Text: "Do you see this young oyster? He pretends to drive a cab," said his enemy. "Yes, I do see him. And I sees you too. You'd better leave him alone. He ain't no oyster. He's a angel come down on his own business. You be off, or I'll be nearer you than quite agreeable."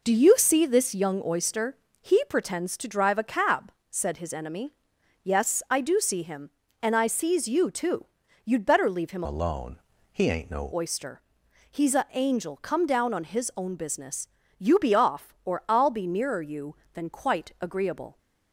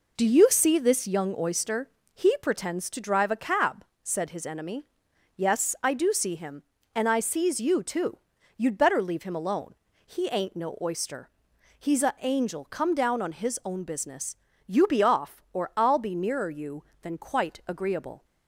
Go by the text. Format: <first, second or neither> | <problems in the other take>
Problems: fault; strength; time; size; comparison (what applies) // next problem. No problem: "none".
second | changes voice from "alone" to "no"; from 9.2 to 10.7 s; 1.5 s long